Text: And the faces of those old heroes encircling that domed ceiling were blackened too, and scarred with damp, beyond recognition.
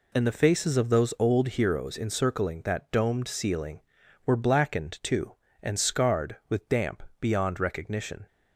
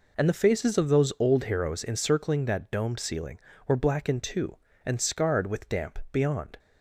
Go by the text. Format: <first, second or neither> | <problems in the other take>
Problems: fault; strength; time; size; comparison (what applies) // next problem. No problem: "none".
first | stops before "recognition"; at 6.5 s